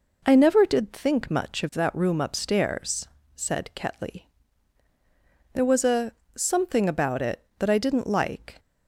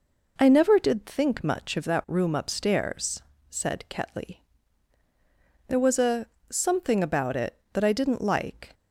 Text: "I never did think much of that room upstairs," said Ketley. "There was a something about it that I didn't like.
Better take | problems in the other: neither | pauses between "a" and "something"; slight; the same in both

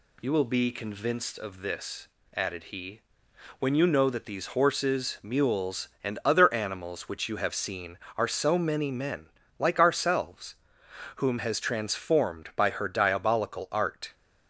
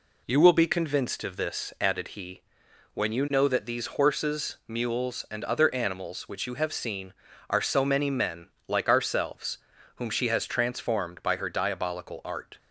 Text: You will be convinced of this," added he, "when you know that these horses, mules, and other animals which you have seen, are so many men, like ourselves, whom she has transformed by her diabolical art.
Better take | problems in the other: second | skips "she"; at 11.3 s

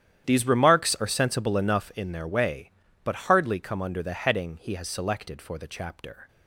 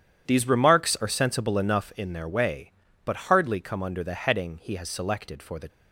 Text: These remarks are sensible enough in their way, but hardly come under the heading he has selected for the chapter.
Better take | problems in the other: first | starts louder than the rest; strong; until 1.2 s; 9.5 dB; strong in the first // stops before "chapter"; at 5.6 s

